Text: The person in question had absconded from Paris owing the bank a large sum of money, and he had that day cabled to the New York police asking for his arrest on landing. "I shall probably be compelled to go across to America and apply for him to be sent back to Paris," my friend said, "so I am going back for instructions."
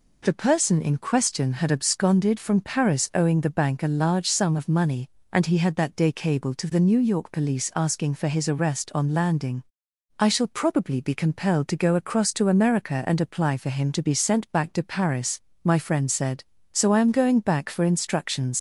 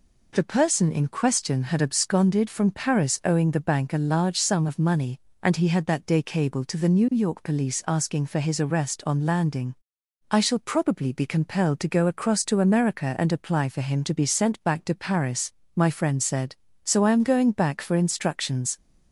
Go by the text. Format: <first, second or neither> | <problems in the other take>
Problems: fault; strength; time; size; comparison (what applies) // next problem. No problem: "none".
second | leaves "instructions" unfinished; at 18.5 s; 55 ms